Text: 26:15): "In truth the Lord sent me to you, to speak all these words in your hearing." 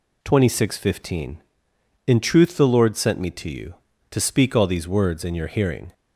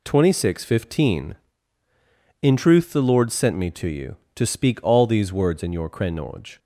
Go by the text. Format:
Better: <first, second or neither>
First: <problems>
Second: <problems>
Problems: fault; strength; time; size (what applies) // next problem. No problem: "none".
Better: first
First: none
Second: says "krenoj" for "hearing"; at 5.9 s